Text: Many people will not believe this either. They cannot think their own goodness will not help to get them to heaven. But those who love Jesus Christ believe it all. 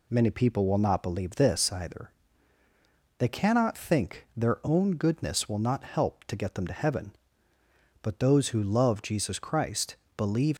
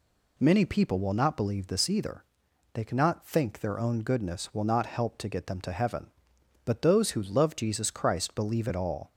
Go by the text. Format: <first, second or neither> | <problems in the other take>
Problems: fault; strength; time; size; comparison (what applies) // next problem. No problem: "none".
second | pauses between "Christ" and "believe"; slight; at 9.9 s; 0.20 s long // stops before "it all"; at 10.5 s